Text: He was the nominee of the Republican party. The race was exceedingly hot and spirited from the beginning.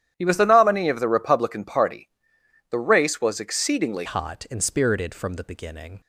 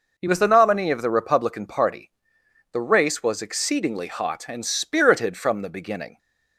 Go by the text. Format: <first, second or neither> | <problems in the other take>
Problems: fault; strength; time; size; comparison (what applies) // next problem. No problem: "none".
second | starts louder than the rest; strong; until 1.1 s; 11 dB // changes voice at "hot"; from 4.0 s on; 2.0 s long